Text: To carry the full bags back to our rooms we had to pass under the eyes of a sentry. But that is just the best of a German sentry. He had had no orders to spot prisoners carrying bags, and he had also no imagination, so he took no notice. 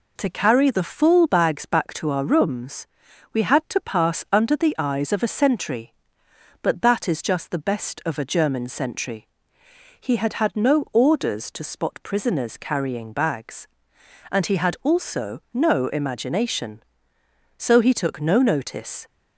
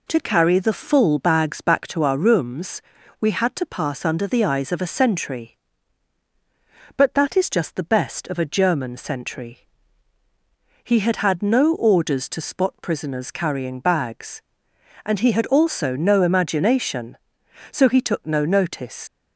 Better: first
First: pauses between "rooms" and "we"; at 2.8 s; 0.44 s long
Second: pauses between "rooms" and "we"; at 2.8 s; 0.38 s long // leaves "notice" unfinished; at 19.0 s; 70 ms

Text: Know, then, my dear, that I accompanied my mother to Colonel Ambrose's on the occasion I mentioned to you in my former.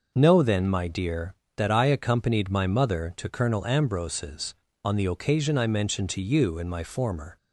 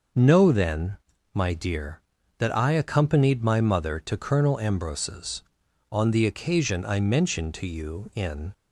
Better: first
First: none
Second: starts louder than the rest; noticeable; until 1.5 s; 6 dB // stops before "my former"; at 8.5 s

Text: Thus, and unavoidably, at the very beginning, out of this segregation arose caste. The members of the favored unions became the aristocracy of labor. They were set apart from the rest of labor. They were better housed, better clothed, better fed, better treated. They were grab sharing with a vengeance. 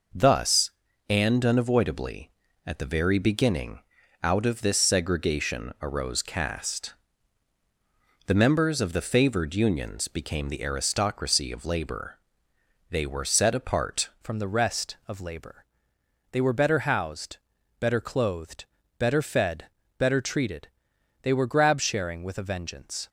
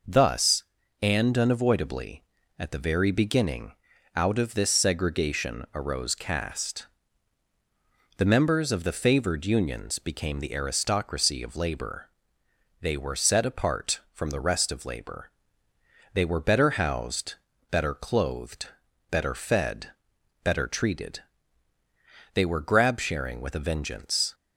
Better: second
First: changes voice at "from"; from 14.2 s on; 8.8 s long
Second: none

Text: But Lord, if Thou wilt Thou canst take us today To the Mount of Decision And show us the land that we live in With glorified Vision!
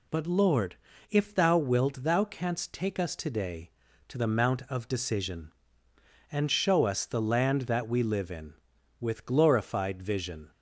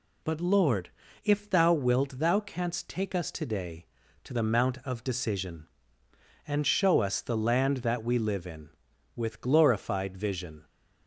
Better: neither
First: none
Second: none

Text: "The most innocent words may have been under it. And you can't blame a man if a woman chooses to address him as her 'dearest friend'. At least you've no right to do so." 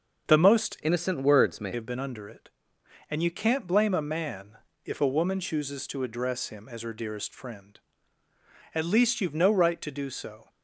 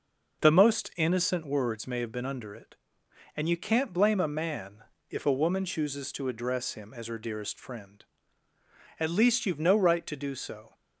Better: second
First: starts louder than the rest; until 1.3 s; 6 dB // changes voice from "innocent" to "may"; from 0.8 to 1.7 s; 0.9 s long // pauses between "man" and "if"; slight; at 4.5 s; 0.28 s long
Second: pauses between "man" and "if"; slight; at 4.8 s; 0.27 s long

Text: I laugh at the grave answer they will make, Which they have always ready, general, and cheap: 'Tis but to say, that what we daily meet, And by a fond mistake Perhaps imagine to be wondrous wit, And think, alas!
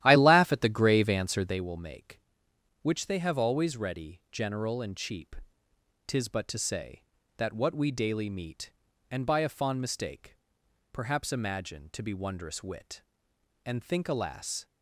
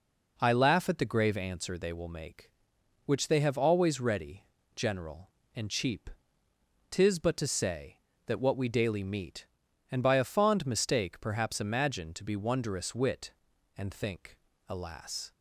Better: second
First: starts louder than the rest; strong; until 1.6 s; 12.5 dB // pauses between "mistake" and "Perhaps"; noticeable; at 10.3 s; 0.56 s long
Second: none

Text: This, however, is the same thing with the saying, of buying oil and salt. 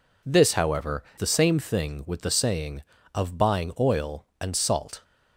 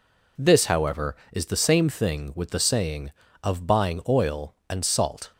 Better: second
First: skips "is"; at 1.1 s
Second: none

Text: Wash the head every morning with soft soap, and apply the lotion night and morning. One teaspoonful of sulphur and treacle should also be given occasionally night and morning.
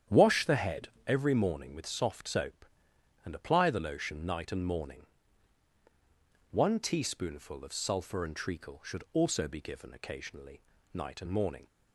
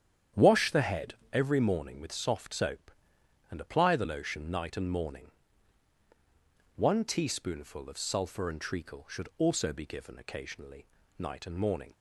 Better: neither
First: starts louder than the rest; strong; until 1.2 s; 9.5 dB // pauses between "head" and "every"; slight; at 0.8 s; 0.18 s long // pauses between "occasionally" and "night"; slight; at 10.6 s; 0.32 s long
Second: starts louder than the rest; strong; until 1.5 s; 9.5 dB // pauses between "head" and "every"; slight; at 1.1 s; 0.18 s long // pauses between "occasionally" and "night"; slight; at 10.8 s; 0.32 s long

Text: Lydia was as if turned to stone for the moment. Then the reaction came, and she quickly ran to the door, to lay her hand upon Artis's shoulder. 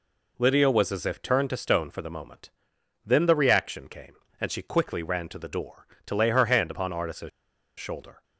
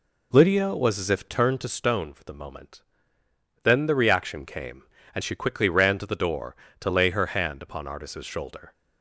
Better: second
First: pauses between "Artis's" and "shoulder"; noticeable; at 7.2 s; 0.50 s long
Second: none

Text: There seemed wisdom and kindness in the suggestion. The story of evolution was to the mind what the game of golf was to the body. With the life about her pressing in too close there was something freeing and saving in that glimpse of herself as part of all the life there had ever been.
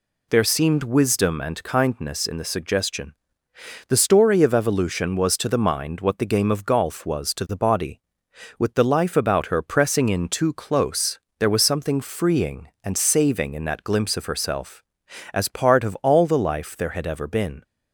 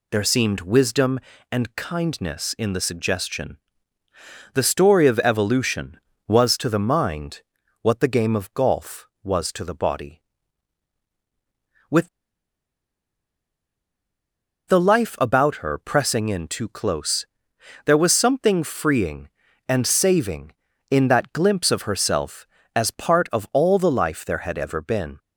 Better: first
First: pauses between "close" and "there"; slight; at 11.1 s; 0.20 s long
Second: pauses between "mind" and "what"; at 7.4 s; 0.40 s long // pauses between "With" and "the"; strong; at 12.0 s; 2.5 s long // pauses between "close" and "there"; noticeable; at 17.2 s; 0.58 s long

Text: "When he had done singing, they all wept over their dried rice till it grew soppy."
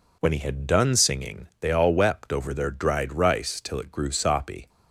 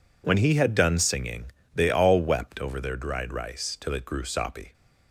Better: neither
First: none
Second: none

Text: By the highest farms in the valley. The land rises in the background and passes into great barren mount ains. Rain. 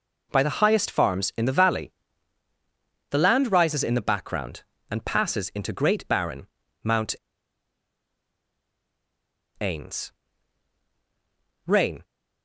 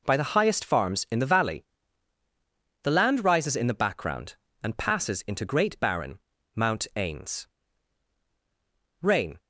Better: second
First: pauses between "barren" and "mount"; at 6.4 s; 0.38 s long // pauses between "mount" and "ains"; strong; at 7.1 s; 2.4 s long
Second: pauses between "barren" and "mount"; at 6.1 s; 0.38 s long

